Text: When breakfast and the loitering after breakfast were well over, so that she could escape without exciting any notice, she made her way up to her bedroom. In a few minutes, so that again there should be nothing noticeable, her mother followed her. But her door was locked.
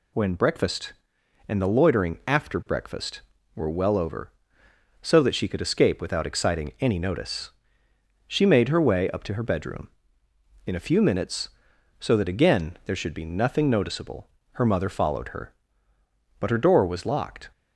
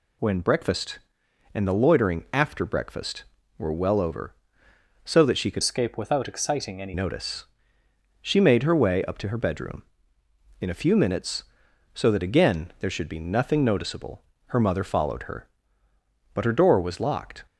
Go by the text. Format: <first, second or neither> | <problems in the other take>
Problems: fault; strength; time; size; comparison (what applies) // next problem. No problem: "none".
first | changes voice from "escape" to "any"; from 5.6 to 6.9 s; 1.3 s long